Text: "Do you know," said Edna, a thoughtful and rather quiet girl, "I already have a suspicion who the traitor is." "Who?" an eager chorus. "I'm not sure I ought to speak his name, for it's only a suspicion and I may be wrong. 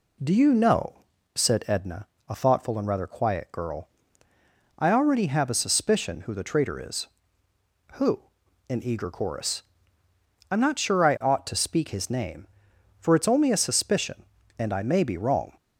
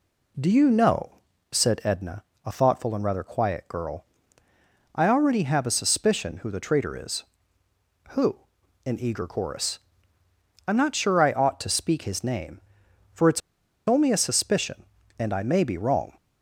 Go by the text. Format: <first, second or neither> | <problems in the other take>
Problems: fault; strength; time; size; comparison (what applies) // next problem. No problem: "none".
first | pauses between "it's" and "only"; noticeable; at 13.4 s; 0.48 s long